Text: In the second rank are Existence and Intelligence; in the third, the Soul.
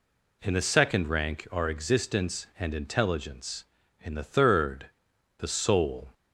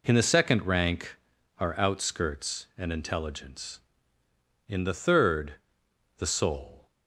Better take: first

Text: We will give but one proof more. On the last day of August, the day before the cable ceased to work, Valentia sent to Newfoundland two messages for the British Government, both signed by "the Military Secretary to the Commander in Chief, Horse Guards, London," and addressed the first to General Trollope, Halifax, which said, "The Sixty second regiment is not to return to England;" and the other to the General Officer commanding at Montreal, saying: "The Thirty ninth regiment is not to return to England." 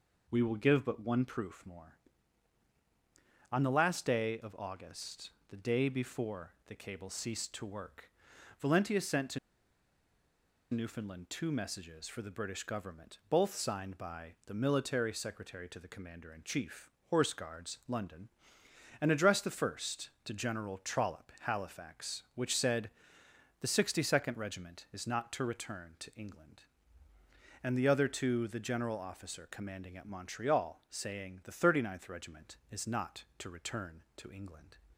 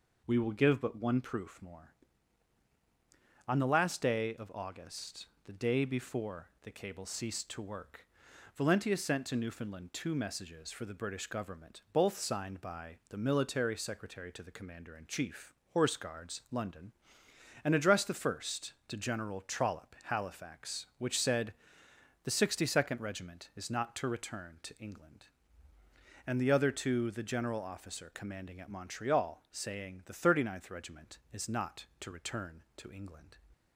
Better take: second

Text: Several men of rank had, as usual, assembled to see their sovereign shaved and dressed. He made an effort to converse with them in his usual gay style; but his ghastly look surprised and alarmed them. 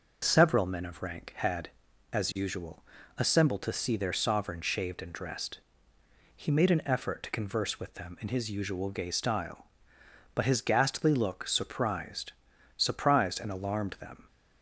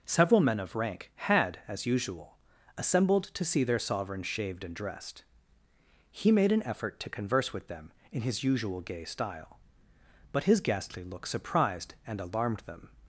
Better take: second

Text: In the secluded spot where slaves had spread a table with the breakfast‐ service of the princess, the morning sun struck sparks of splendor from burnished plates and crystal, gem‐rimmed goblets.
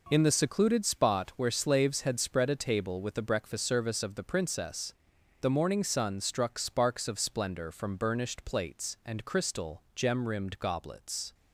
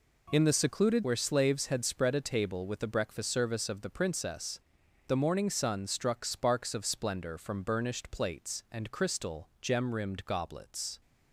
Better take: first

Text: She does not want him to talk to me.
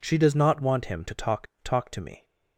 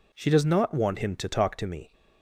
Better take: second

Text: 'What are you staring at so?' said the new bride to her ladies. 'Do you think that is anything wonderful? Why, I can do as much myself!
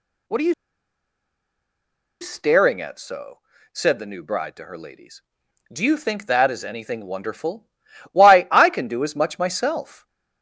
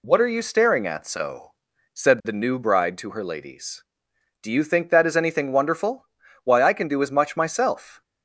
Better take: second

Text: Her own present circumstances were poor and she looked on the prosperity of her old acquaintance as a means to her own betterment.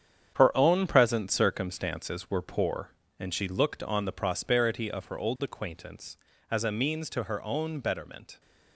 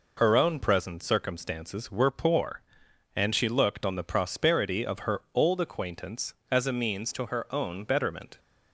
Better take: second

